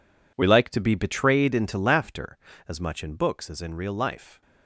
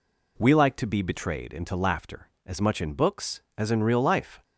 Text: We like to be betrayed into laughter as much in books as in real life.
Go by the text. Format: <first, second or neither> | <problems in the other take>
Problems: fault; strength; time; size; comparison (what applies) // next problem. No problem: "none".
second | gets quieter; strong; throughout; 13 dB